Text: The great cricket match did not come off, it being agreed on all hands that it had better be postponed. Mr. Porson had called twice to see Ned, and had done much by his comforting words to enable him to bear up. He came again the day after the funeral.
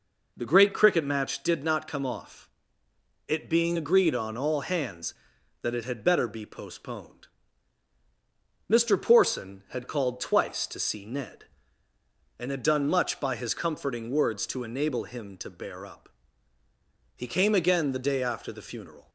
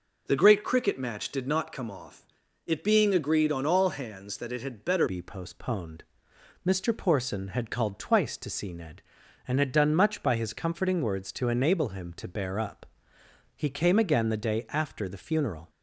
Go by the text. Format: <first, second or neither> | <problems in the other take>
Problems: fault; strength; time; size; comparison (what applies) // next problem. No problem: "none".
first | changes voice at "be"; from 5.0 s on; 10.6 s long